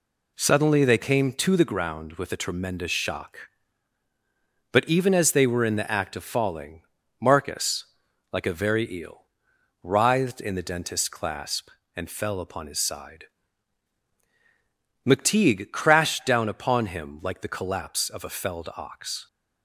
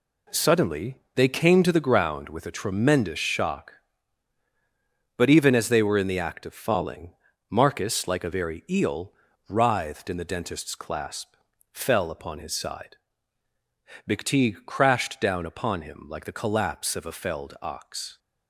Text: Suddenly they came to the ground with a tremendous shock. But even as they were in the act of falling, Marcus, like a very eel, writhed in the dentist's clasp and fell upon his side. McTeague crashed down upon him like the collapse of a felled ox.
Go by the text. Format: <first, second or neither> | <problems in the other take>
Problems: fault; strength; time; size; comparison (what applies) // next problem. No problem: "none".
first | skips "and"; at 11.5 s